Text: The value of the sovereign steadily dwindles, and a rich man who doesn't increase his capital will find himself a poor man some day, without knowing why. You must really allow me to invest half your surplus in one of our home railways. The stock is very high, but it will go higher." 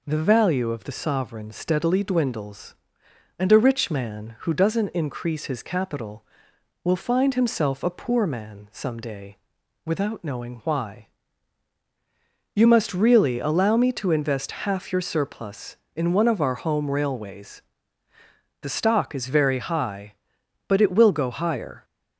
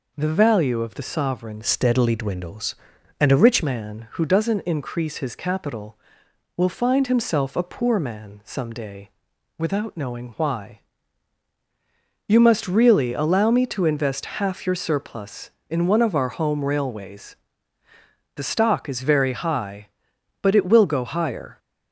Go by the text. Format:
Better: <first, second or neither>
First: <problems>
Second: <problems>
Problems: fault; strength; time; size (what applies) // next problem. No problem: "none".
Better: first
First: none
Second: changes voice from "steadily" to "rich"; from 1.6 to 3.6 s; 2.0 s long